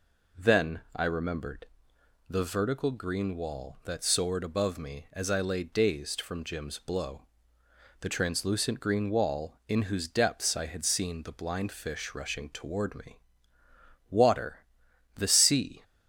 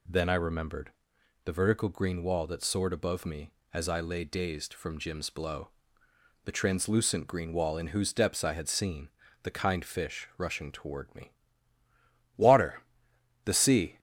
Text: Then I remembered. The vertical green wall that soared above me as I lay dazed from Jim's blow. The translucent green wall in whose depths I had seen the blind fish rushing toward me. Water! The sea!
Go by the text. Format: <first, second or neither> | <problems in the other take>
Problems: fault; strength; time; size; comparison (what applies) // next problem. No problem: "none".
first | pauses between "seen" and "the"; slight; at 9.0 s; 0.34 s long // says "kind" for "blind"; at 9.5 s